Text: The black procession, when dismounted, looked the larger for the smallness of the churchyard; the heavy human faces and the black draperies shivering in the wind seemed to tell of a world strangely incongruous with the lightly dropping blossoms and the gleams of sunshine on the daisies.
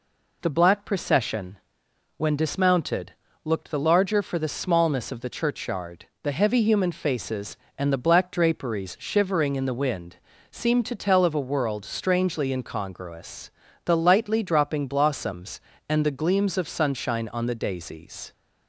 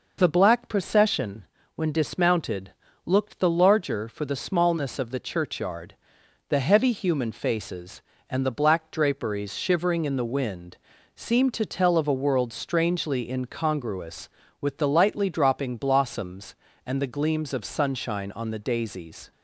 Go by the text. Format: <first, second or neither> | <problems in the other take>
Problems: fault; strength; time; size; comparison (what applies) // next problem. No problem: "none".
second | pauses between "wind" and "seemed"; slight; at 10.1 s; 0.34 s long; also in the second // skips "with"; at 13.6 s